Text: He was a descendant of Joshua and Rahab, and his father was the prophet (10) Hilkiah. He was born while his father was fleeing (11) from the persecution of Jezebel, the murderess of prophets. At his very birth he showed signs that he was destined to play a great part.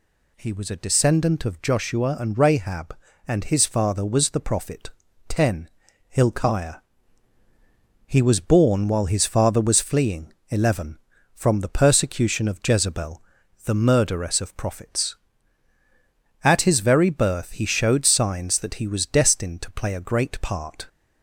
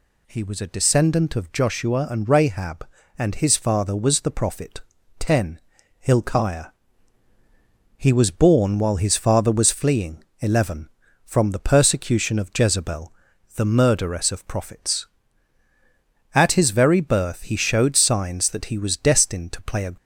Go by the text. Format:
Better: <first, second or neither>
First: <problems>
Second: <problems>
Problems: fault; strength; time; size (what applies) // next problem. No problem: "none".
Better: first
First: none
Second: stops before "great part"; at 19.9 s